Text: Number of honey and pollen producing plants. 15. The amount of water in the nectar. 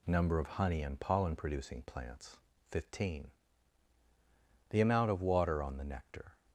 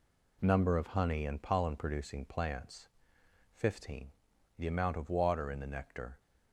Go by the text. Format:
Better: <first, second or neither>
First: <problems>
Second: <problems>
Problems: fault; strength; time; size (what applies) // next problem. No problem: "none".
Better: second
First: says "on" for "in"; at 5.6 s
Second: none